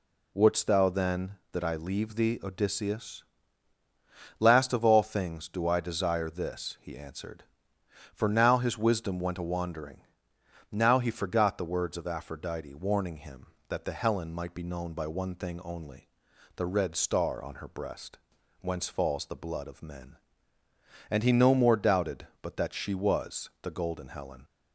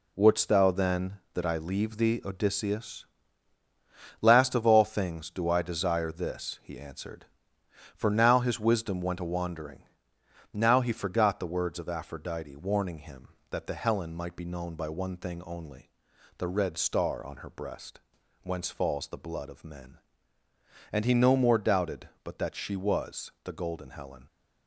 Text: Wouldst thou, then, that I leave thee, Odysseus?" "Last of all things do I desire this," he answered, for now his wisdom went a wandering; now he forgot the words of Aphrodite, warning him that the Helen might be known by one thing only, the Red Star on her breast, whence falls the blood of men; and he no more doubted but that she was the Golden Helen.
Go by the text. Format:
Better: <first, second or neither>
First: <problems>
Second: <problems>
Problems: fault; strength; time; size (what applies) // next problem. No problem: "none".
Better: first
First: none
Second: gets quieter; throughout; 6.5 dB